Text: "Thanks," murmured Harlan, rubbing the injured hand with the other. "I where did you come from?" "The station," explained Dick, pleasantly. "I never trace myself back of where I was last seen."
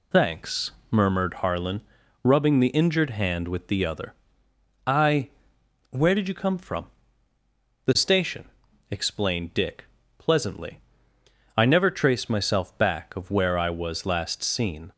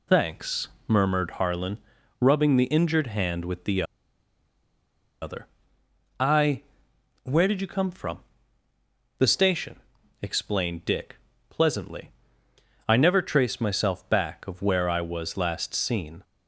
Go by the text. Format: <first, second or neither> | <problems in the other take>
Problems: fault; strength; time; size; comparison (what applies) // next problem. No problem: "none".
first | pauses between "the" and "other"; strong; at 3.8 s; 1.3 s long // pauses between "I" and "where"; noticeable; at 6.6 s; 0.58 s long; noticeable in the first